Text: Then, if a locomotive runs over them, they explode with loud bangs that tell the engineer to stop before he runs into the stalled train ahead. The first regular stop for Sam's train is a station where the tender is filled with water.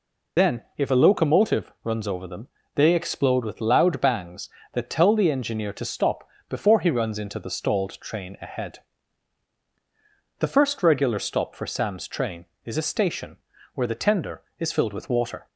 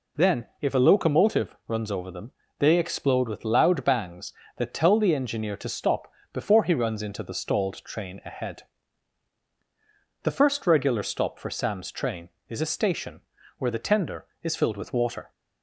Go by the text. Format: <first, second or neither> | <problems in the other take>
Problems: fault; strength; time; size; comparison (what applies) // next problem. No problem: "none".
second | loses the start of "Then"; at 0.3 s; 40 ms // pauses between "stop" and "before"; slight; at 6.2 s; 0.20 s long; slight in the second // pauses between "station" and "where"; at 13.3 s; 0.38 s long; also in the second